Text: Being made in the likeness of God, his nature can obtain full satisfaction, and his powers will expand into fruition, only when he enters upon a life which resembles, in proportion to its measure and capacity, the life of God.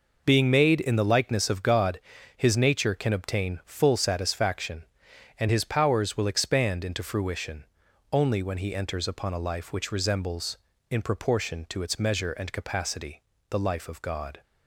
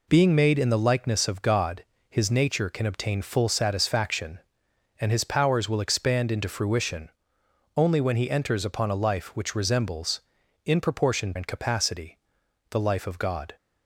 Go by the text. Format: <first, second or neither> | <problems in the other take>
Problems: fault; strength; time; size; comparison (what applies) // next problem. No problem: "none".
first | skips "to its measure"; at 11.3 s